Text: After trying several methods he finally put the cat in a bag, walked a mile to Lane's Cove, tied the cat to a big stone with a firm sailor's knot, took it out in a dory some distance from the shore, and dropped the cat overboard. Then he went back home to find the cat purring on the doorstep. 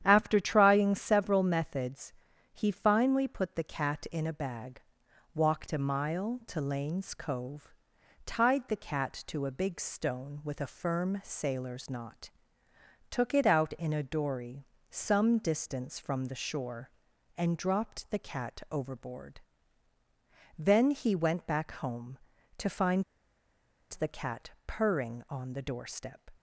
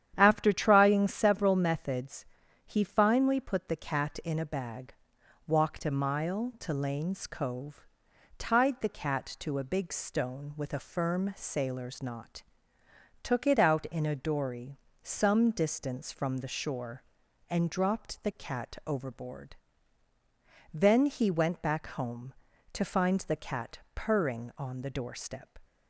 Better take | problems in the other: second | starts louder than the rest; strong; until 1.0 s; 9.5 dB; strong in the second // pauses between "methods" and "he"; at 2.1 s; 0.40 s long; also in the second // pauses between "dory" and "some"; slight; at 14.6 s; 0.24 s long; slight in the second // pauses between "find" and "the"; noticeable; at 23.0 s; 0.89 s long // pauses between "cat" and "purring"; slight; at 24.4 s; 0.18 s long; slight in the second

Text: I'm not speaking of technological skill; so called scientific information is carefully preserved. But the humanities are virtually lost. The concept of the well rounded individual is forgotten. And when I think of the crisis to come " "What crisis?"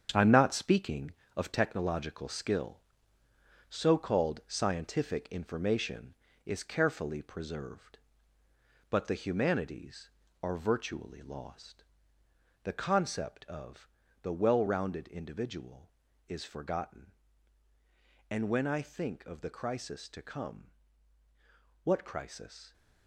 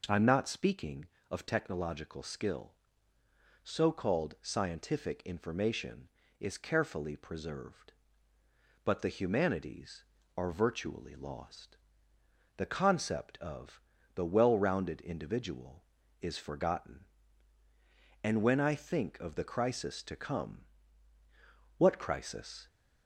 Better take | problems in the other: second | gets quieter; strong; throughout; 13 dB // pauses between "of" and "the"; slight; at 13.8 s; 0.36 s long; slight in the second

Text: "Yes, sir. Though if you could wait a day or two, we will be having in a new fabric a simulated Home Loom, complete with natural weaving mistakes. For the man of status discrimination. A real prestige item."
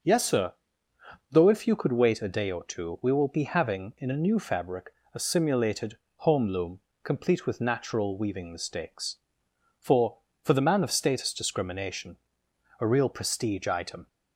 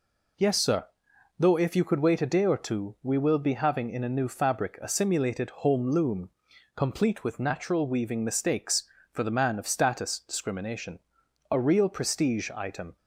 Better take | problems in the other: second | starts louder than the rest; noticeable; until 1.7 s; 6 dB // pauses between "fabric" and "a"; slight; at 4.9 s; 0.20 s long // pauses between "simulated" and "Home"; slight; at 5.9 s; 0.20 s long // says "For" twice; at 10.4 s

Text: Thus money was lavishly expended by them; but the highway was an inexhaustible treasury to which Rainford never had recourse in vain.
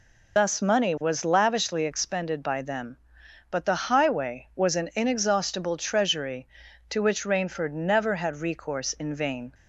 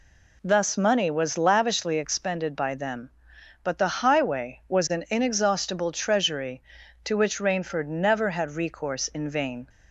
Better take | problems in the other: second | loses the start of "Thus"; at 0.3 s; 105 ms

